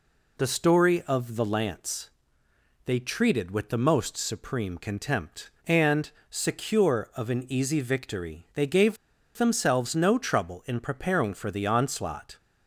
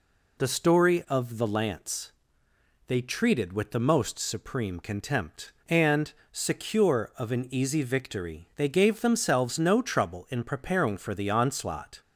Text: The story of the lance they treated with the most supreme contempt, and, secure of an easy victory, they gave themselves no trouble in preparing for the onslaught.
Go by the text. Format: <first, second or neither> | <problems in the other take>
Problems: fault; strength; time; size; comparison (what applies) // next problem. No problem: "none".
second | pauses between "lance" and "they"; noticeable; at 2.1 s; 0.74 s long; noticeable in the second // pauses between "gave" and "themselves"; at 8.9 s; 0.40 s long